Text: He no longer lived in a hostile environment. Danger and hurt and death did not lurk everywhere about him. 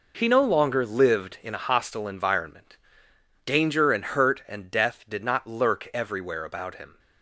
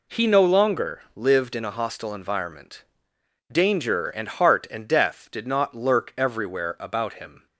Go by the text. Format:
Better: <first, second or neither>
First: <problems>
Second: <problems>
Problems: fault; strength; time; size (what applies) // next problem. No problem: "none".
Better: first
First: none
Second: says "heart" for "hurt"; at 4.2 s